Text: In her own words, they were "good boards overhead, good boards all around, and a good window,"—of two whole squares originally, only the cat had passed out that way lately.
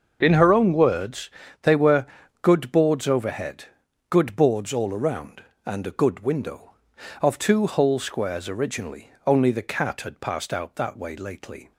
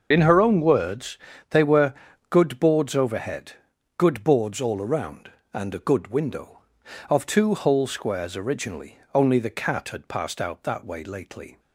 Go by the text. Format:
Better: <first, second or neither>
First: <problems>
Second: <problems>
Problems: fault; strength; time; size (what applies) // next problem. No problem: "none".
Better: first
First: starts louder than the rest; until 1.2 s; 6.5 dB // pauses between "were" and "good"; at 2.0 s; 0.38 s long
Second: loses the start of "In"; at 0.1 s; 25 ms // starts louder than the rest; until 1.1 s; 6.5 dB // pauses between "were" and "good"; at 1.9 s; 0.38 s long